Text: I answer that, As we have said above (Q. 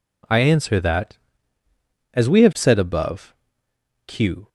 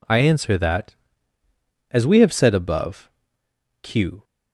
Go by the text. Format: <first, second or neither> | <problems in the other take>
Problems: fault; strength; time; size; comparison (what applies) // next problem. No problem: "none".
neither | none